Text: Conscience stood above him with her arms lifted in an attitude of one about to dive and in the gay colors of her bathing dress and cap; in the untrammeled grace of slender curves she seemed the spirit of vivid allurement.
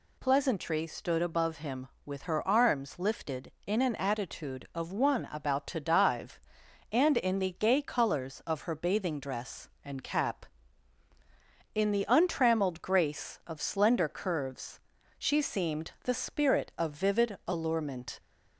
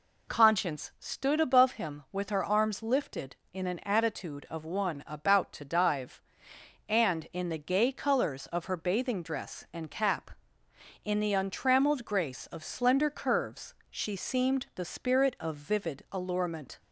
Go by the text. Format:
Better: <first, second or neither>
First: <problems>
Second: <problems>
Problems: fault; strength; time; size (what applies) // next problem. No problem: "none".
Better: second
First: says "Pleasantry" for "Conscience"; at 0.1 s // pauses between "curves" and "she"; at 14.7 s; 0.40 s long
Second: pauses between "curves" and "she"; slight; at 13.7 s; 0.16 s long